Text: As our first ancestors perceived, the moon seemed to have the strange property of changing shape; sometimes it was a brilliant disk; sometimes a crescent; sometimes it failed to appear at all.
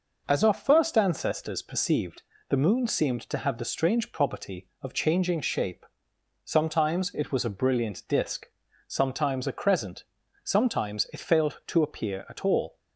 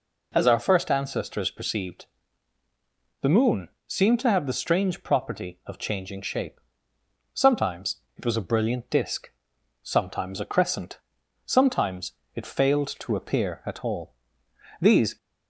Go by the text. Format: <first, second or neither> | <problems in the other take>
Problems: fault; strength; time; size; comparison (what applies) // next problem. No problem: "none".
first | pauses between "moon" and "seemed"; slight; at 3.6 s; 0.18 s long // pauses between "sometimes" and "it"; slight; at 7.9 s; 0.20 s long // pauses between "sometimes" and "it"; slight; at 12.1 s; 0.22 s long // goes on to say "These"; slight; from 14.8 s on; 0.36 s long